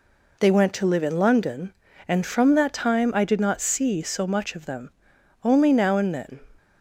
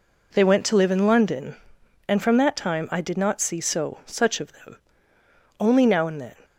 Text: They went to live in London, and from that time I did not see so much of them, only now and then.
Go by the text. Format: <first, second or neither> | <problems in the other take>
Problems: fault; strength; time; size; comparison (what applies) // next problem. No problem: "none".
first | says "such" for "much"; at 4.0 s